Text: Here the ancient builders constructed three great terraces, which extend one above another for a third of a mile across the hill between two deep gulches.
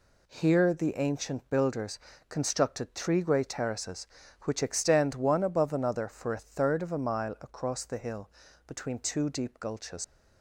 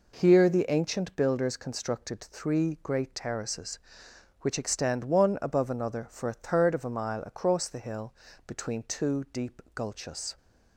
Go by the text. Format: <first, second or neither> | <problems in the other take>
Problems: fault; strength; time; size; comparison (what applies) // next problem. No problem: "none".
second | pauses between "builders" and "constructed"; slight; at 1.9 s; 0.30 s long // pauses between "hill" and "between"; at 8.2 s; 0.38 s long; slight in the second // leaves "gulches" unfinished; at 10.0 s; 105 ms